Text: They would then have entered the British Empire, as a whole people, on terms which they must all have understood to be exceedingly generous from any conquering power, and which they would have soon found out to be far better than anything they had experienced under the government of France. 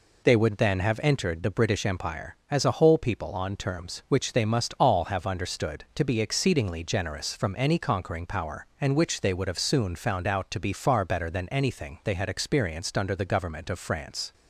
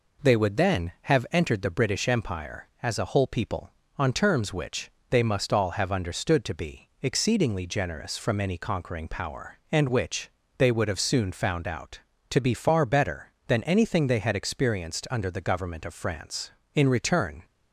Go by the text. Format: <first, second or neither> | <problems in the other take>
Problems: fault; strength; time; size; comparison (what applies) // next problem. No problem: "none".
first | pauses between "which" and "they"; slight; at 4.8 s; 0.20 s long // pauses between "which" and "they"; slight; at 10.2 s; 0.28 s long // goes on to say "In return"; noticeable; from 16.7 s on; 0.70 s long